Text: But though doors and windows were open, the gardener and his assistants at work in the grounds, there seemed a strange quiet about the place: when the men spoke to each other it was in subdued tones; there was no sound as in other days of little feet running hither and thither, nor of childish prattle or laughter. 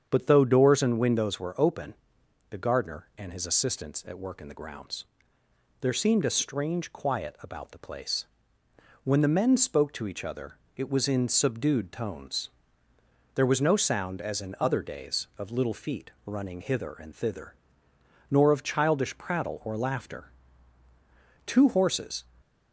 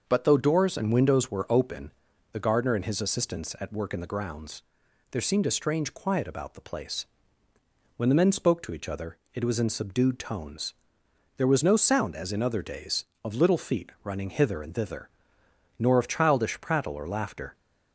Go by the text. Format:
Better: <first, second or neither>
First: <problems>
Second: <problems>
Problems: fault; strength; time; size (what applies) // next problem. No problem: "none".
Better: second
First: starts louder than the rest; strong; until 1.1 s; 8 dB // pauses between "other" and "it"; slight; at 10.5 s; 0.22 s long // goes on to say "Two horses"; noticeable; from 21.4 s on; 0.78 s long // stays silent after the last word; slight; from 22.2 s on; 0.5 s long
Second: starts louder than the rest; noticeable; until 1.0 s; 6 dB // pauses between "other" and "it"; slight; at 9.1 s; 0.16 s long